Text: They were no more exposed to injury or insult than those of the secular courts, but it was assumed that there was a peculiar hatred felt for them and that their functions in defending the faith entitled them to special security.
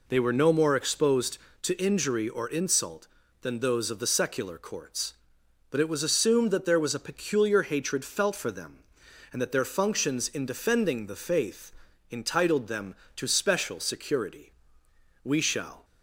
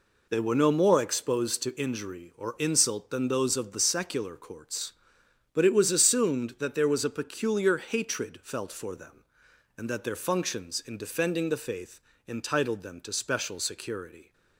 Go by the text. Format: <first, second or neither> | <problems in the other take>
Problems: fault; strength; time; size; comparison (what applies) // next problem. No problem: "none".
second | pauses between "faith" and "entitled"; at 11.7 s; 0.38 s long; slight in the second // goes on to say "We shall"; from 15.2 s on; 0.60 s long